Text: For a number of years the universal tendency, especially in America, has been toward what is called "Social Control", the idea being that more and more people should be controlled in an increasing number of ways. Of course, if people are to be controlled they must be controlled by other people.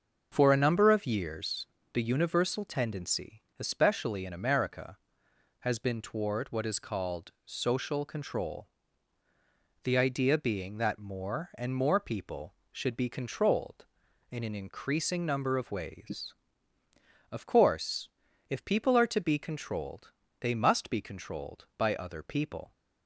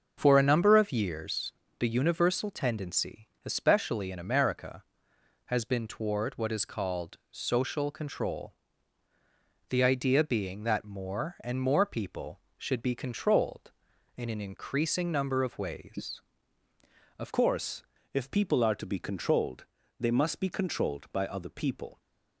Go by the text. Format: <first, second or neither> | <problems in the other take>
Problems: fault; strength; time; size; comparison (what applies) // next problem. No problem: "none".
first | starts louder than the rest; until 1.1 s; 6.5 dB; also in the first // pauses between "years" and "the"; slight; at 1.5 s; 0.26 s long; slight in the first // changes voice at "course"; from 17.3 s on; 4.7 s long // pauses between "controlled" and "they"; slight; at 19.6 s; 0.34 s long; slight in the first